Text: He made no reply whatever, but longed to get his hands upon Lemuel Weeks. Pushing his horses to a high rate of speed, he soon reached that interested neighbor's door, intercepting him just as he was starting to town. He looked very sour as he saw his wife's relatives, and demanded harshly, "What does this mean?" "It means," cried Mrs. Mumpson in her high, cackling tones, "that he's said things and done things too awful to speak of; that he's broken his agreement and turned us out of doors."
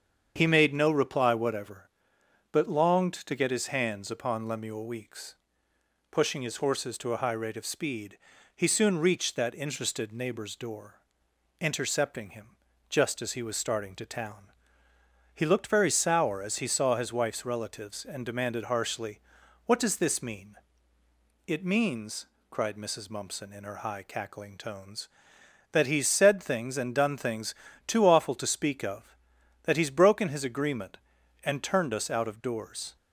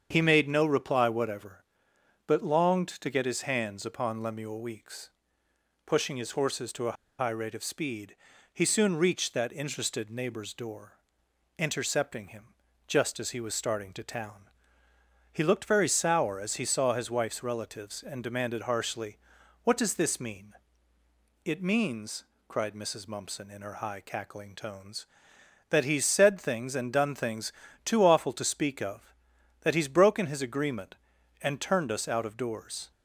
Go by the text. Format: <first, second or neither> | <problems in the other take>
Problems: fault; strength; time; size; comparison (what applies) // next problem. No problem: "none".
first | starts louder than the rest; strong; until 1.1 s; 7.5 dB; strong in the first // pauses between "a" and "high"; slight; at 6.9 s; 0.24 s long // pauses between "him" and "just"; at 12.4 s; 0.42 s long; also in the first // pauses between "things" and "too"; slight; at 27.5 s; 0.32 s long; slight in the first